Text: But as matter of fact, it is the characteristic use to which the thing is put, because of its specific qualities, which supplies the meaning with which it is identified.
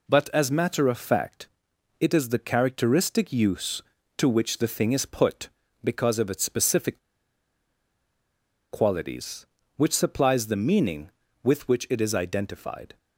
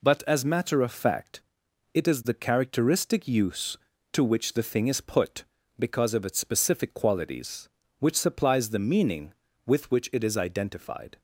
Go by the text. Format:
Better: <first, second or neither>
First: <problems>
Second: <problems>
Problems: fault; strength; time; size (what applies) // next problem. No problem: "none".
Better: second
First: pauses between "specific" and "qualities"; strong; at 6.9 s; 1.7 s long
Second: none